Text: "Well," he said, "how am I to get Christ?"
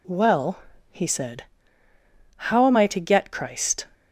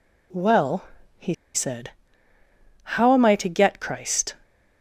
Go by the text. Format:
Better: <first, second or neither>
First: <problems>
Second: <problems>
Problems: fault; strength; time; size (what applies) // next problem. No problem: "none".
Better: first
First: none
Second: pauses between "he" and "said"; slight; at 1.3 s; 0.21 s long